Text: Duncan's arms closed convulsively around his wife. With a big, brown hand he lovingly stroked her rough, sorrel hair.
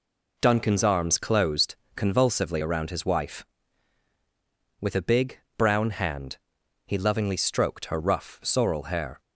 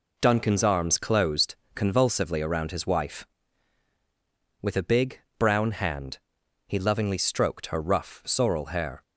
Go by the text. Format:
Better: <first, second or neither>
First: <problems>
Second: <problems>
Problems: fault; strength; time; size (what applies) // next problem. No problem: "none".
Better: neither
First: pauses between "closed" and "convulsively"; slight; at 1.7 s; 0.20 s long // pauses between "hand" and "he"; noticeable; at 6.3 s; 0.48 s long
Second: pauses between "closed" and "convulsively"; slight; at 1.5 s; 0.19 s long // pauses between "hand" and "he"; noticeable; at 6.1 s; 0.48 s long